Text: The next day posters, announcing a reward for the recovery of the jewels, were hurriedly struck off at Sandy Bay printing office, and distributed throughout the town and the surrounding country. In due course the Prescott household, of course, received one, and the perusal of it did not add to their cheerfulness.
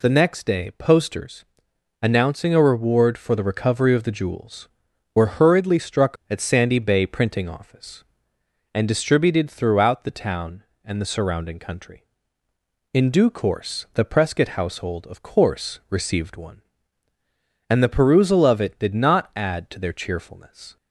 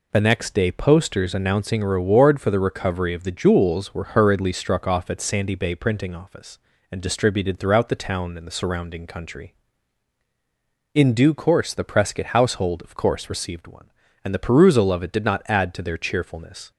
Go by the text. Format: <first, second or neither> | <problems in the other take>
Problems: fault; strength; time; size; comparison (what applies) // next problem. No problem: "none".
second | skips "off"; at 6.2 s